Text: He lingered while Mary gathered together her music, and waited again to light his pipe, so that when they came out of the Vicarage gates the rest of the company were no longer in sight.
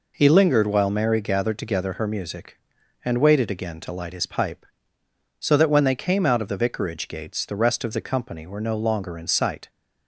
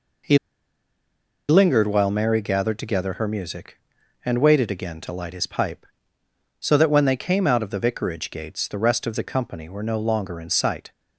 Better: first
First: none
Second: pauses between "He" and "lingered"; at 0.3 s; 1.1 s long

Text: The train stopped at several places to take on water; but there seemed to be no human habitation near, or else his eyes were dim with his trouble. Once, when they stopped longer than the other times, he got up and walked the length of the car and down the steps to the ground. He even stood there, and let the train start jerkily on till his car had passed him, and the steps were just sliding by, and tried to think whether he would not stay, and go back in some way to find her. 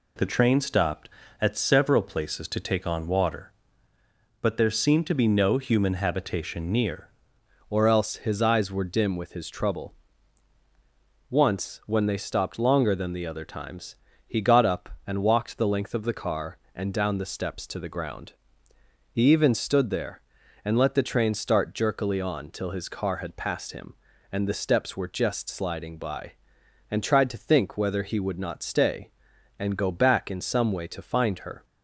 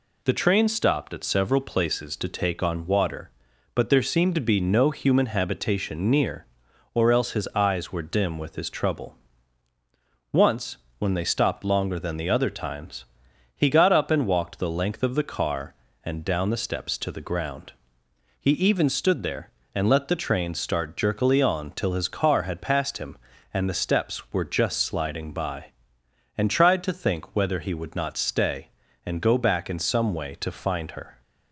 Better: second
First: changes voice at "or"; from 7.7 s on; 23.9 s long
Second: none

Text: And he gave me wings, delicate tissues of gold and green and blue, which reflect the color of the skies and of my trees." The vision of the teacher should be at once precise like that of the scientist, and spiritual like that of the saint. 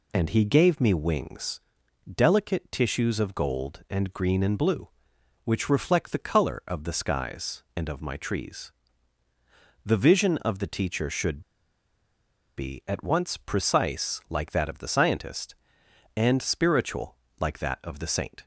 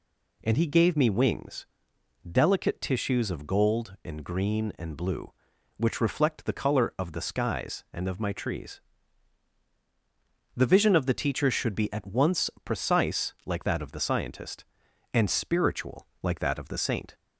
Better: second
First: pauses between "should" and "be"; at 11.3 s; 1.1 s long // pauses between "spiritual" and "like"; slight; at 17.1 s; 0.24 s long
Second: pauses between "spiritual" and "like"; slight; at 16.0 s; 0.16 s long

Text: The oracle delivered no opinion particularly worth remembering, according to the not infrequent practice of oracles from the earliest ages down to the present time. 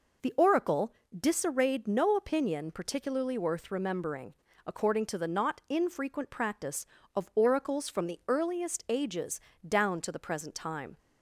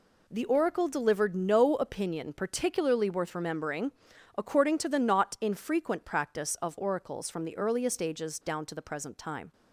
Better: second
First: says "disarrayed" for "delivered"; at 1.1 s // pauses between "ages" and "down"; slight; at 9.3 s; 0.28 s long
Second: none

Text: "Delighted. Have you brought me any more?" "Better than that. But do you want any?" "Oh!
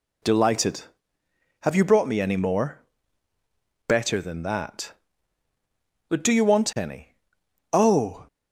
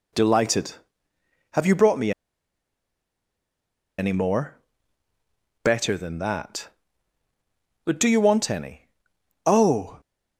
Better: first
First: none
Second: pauses between "me" and "any"; strong; at 2.1 s; 1.8 s long

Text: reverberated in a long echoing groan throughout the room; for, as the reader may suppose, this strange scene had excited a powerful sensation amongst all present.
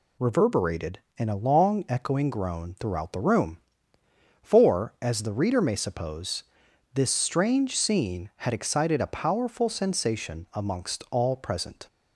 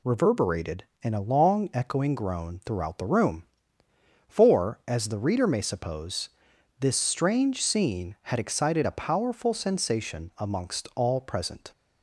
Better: neither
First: none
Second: none

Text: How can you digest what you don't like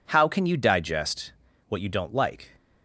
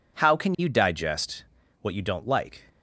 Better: neither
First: pauses between "digest" and "what"; at 1.3 s; 0.38 s long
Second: pauses between "digest" and "what"; at 1.4 s; 0.40 s long

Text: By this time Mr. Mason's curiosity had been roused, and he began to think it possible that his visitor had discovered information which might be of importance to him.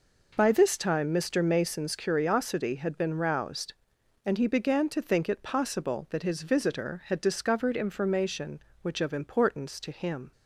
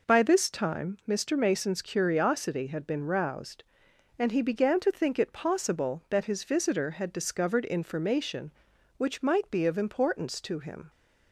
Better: second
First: skips "might be"; at 8.9 s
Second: none

